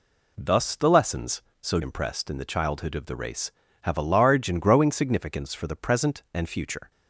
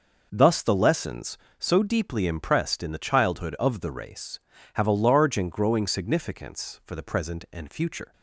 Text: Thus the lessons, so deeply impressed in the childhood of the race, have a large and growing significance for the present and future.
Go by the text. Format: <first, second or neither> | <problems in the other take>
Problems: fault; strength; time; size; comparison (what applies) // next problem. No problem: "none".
second | skips "deeply"; at 1.8 s